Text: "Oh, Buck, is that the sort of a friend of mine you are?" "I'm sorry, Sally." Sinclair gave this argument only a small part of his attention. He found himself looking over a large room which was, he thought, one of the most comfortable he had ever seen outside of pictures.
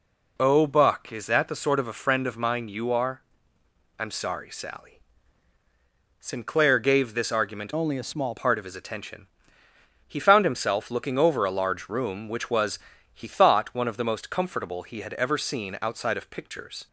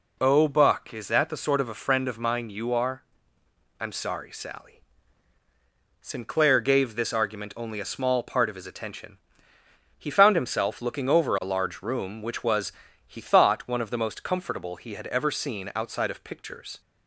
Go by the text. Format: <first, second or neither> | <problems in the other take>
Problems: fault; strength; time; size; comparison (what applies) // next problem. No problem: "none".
second | changes voice from "only" to "small"; from 7.7 to 8.3 s; 0.6 s long